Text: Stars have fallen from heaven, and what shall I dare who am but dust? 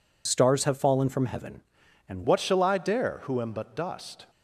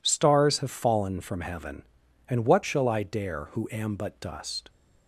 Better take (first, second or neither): second